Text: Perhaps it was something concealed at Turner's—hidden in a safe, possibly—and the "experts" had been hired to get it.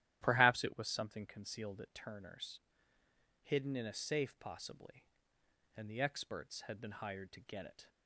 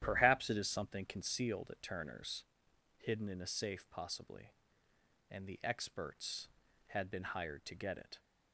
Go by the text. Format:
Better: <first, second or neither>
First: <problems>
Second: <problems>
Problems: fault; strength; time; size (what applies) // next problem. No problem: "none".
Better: first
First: starts louder than the rest; strong; until 1.2 s; 12.5 dB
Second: starts louder than the rest; strong; until 1.0 s; 11 dB // says "is" for "was"; at 0.5 s